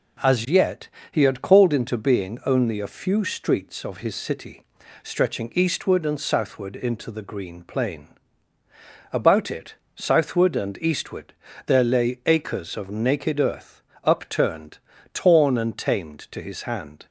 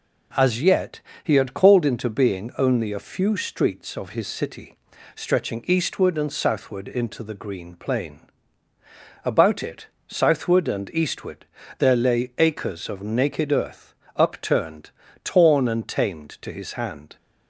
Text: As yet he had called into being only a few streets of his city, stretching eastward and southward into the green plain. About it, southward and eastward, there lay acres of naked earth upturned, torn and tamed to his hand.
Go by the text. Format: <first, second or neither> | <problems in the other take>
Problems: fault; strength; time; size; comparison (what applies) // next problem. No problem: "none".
neither | pauses between "yet" and "he"; slight; the same in both // pauses between "earth" and "upturned"; slight; the same in both